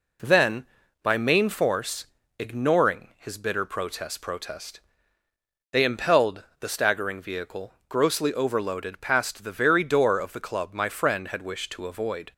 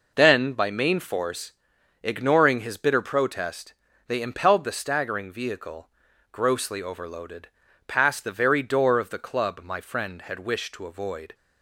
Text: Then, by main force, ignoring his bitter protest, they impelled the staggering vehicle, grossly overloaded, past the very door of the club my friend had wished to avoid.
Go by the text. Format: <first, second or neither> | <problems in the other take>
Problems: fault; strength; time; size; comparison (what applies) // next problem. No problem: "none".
second | says "protest" twice; at 4.2 s // pauses between "impelled" and "the"; slight; at 6.4 s; 0.16 s long